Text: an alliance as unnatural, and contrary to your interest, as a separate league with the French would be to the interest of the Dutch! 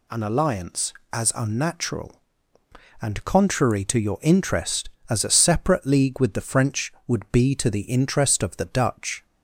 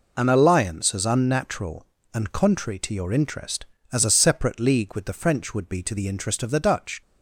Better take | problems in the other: neither | none

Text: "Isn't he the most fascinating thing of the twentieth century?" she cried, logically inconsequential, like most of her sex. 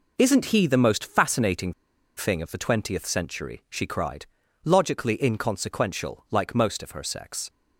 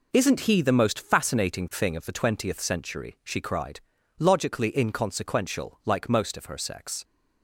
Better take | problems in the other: second | pauses between "fascinating" and "thing"; at 1.7 s; 0.43 s long

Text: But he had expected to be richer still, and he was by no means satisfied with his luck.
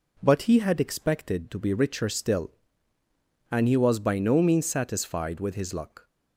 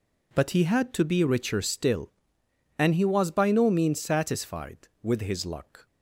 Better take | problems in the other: first | skips "expected"; at 0.9 s

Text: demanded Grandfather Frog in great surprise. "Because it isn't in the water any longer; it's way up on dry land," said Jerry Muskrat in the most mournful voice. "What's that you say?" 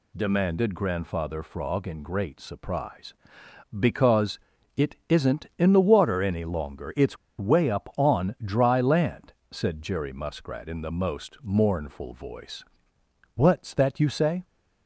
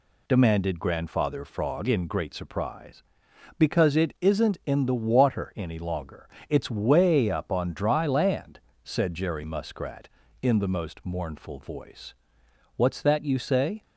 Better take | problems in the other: second | pauses between "Because" and "it"; slight; at 4.4 s; 0.36 s long // pauses between "it's" and "way"; slight; at 7.1 s; 0.22 s long

